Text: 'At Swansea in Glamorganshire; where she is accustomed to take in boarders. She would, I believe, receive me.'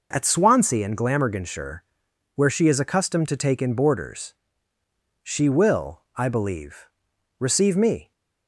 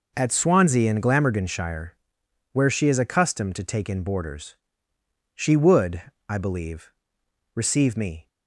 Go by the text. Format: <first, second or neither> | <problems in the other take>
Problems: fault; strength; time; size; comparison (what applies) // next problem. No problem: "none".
second | says "will" for "would"; at 5.4 s